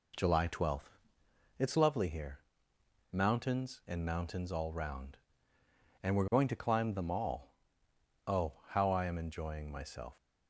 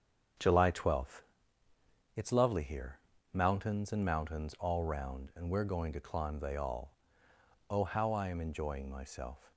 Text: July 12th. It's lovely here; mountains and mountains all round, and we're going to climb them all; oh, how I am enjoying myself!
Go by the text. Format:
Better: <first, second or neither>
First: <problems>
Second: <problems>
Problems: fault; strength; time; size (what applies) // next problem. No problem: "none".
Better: first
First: none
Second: starts louder than the rest; until 2.2 s; 7 dB // says "they" for "them"; at 6.3 s